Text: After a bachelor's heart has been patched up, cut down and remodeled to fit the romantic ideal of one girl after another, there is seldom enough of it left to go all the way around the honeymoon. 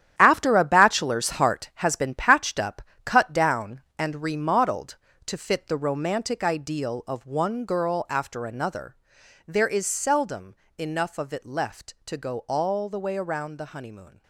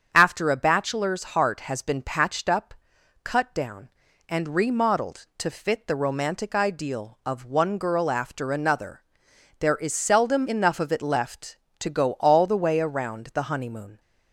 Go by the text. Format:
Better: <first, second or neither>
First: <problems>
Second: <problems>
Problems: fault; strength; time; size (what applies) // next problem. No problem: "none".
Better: second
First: gets quieter; strong; throughout; 10 dB // starts louder than the rest; strong; until 1.1 s; 11 dB // pauses between "seldom" and "enough"; slight; at 10.5 s; 0.24 s long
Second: starts louder than the rest; strong; until 1.1 s; 7 dB